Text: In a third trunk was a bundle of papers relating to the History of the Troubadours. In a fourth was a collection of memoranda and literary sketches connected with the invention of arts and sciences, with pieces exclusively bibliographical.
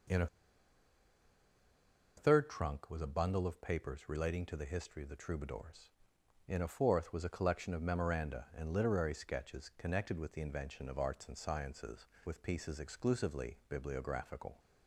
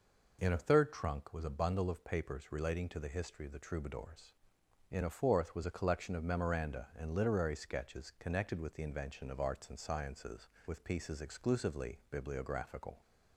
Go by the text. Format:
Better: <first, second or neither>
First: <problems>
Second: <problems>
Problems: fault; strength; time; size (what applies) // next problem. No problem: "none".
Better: second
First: pauses between "a" and "third"; strong; at 0.2 s; 1.9 s long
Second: none